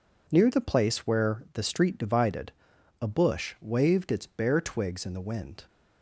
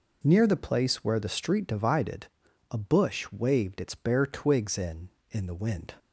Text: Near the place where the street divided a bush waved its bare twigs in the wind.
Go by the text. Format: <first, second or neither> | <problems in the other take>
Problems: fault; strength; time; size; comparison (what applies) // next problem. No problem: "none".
first | pauses between "divided" and "a"; noticeable; at 2.2 s; 0.46 s long; noticeable in the first // says "in" twice; at 5.3 s